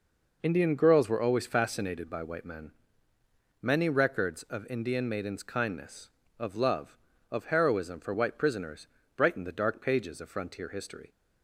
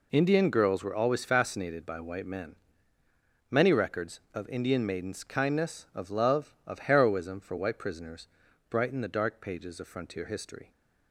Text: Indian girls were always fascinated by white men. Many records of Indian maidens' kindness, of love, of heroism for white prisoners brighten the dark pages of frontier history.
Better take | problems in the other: neither | pauses between "prisoners" and "brighten"; the same in both

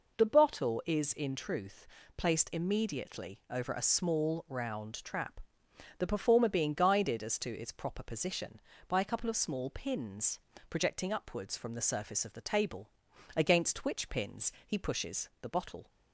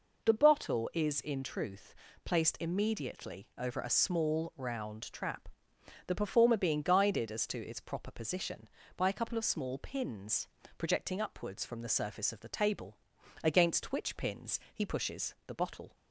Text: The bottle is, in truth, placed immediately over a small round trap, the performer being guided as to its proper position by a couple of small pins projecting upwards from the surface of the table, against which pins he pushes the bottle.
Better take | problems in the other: neither | pauses between "pins" and "projecting"; slight; the same in both

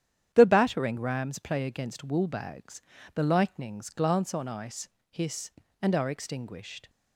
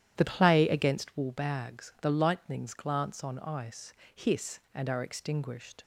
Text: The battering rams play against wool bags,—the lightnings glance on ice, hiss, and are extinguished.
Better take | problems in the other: first | starts louder than the rest; strong; until 1.1 s; 11 dB; strong in the first // skips "battering rams"; at 0.2 s

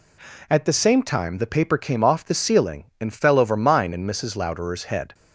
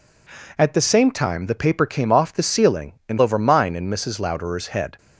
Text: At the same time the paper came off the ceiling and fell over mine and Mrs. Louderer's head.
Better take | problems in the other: first | skips "fell"; at 3.2 s

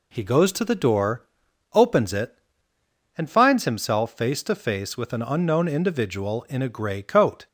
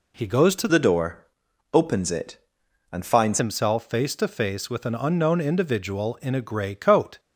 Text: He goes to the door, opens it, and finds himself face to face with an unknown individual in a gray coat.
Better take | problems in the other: first | changes voice from "the" to "finds"; from 0.6 to 3.3 s; 2.7 s long

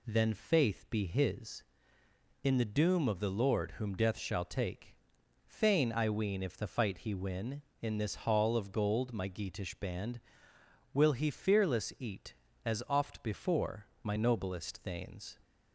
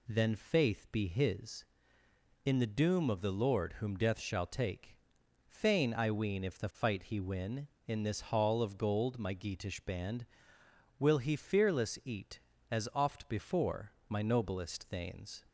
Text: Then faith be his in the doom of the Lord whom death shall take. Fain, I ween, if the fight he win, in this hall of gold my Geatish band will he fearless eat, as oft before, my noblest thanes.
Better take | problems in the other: neither | none

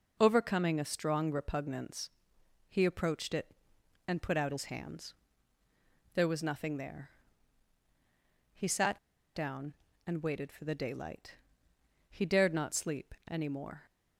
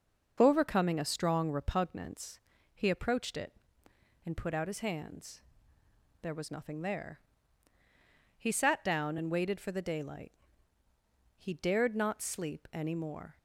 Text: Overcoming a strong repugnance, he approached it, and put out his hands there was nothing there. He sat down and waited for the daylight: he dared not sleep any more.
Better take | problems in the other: second | pauses between "hands" and "there"; at 5.1 s; 1.0 s long; noticeable in the second // pauses between "sat" and "down"; at 8.9 s; 0.38 s long

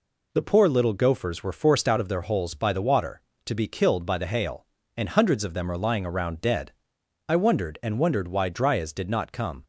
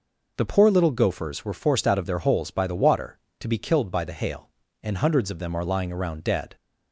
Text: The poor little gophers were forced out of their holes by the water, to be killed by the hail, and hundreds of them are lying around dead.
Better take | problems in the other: second | goes on to say "I wondered and wondered why Dryas did not come"; strong; from 7.2 s on; 2.3 s long

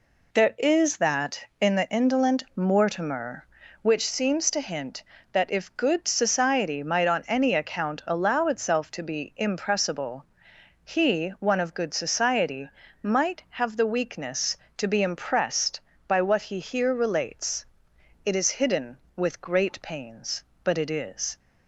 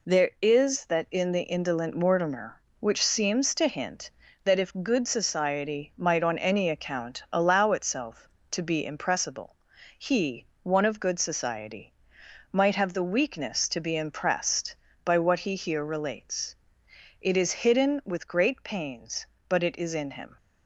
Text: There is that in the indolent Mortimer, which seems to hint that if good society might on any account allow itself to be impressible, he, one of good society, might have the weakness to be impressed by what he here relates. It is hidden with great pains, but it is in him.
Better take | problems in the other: second | stops before "in him"; at 21.3 s

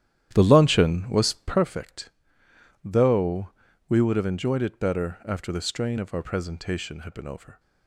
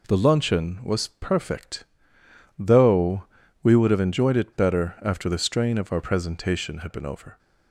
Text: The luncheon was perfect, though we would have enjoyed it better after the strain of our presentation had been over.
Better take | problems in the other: second | starts louder than the rest; strong; until 1.7 s; 11.5 dB // pauses between "though" and "we"; at 3.4 s; 0.40 s long; also in the second

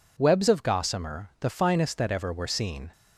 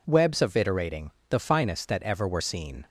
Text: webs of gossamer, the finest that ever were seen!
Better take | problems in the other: first | says "iterating" for "gossamer"; at 0.5 s

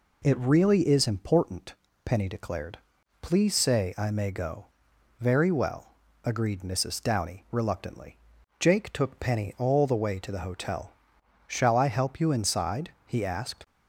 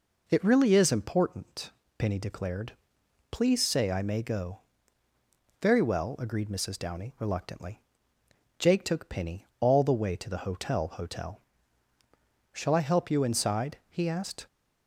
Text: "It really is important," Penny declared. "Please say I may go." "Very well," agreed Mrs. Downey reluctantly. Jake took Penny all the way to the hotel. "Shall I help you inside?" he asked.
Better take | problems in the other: first | says "hotel" twice; at 10.8 s

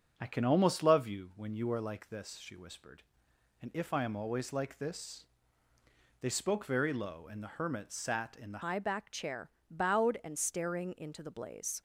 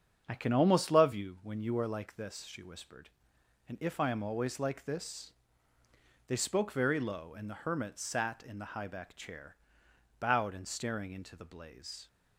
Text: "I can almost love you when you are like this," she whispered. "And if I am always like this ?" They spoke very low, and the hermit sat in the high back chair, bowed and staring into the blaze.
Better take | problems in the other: second | starts louder than the rest; strong; until 1.1 s; 8 dB; strong in the second // changes voice at "high"; from 8.6 s on; 3.2 s long

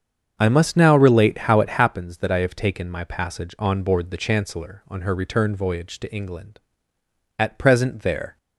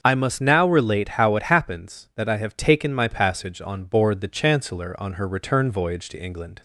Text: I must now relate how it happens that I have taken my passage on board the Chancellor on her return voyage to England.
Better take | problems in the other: second | starts louder than the rest; strong; until 1.3 s; 7.5 dB; also in the second // goes on to say "At present there"; noticeable; from 7.3 s on; 0.98 s long

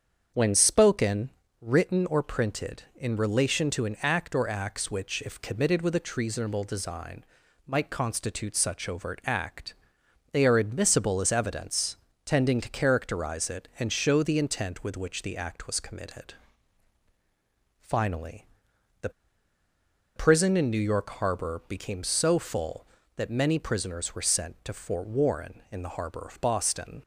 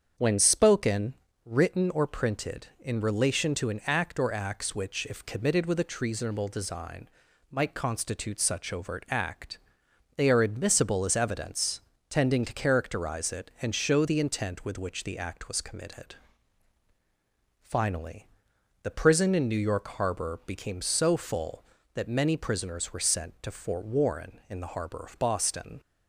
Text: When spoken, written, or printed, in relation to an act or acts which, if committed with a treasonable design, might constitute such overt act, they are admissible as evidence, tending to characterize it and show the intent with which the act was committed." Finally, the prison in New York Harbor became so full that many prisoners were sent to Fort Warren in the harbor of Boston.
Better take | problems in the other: second | starts louder than the rest; strong; until 1.6 s; 7 dB; strong in the second // pauses between "the" and "prison"; at 19.1 s; 1.0 s long

